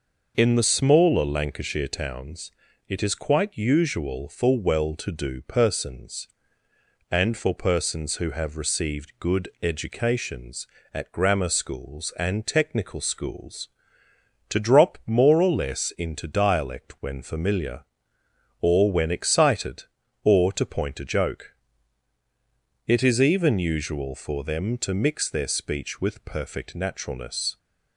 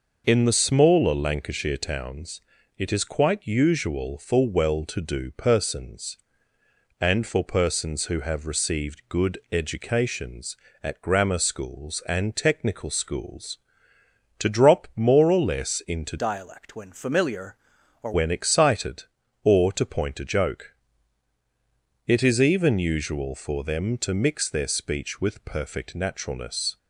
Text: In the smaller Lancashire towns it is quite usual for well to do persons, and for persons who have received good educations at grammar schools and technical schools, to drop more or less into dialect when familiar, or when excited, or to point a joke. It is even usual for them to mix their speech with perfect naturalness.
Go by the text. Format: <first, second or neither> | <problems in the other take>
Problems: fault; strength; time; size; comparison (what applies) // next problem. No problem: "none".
first | pauses between "towns" and "it"; at 2.4 s; 0.38 s long; also in the first // pauses between "good" and "educations"; slight; at 9.3 s; 0.16 s long; slight in the first // changes voice from "dialect" to "or"; from 16.1 to 18.1 s; 2.0 s long